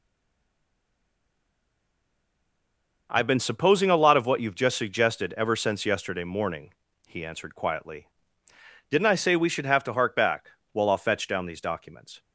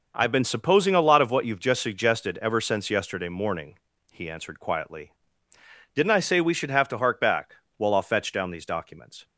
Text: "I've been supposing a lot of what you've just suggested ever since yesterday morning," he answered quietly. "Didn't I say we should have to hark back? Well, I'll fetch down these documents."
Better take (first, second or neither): second